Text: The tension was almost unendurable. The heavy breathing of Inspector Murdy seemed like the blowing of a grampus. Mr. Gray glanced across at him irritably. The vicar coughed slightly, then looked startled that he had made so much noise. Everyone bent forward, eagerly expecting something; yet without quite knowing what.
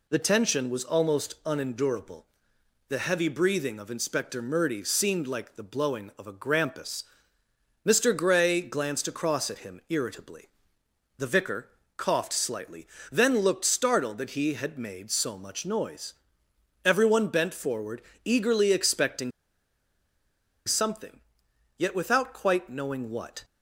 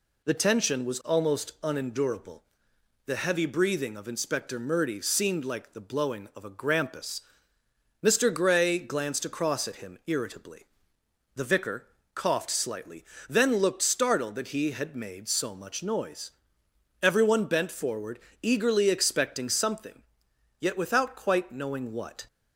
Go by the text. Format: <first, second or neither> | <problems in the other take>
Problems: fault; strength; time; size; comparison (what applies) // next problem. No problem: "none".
second | pauses between "vicar" and "coughed"; slight; at 11.6 s; 0.28 s long; slight in the second // pauses between "expecting" and "something"; strong; at 19.3 s; 1.3 s long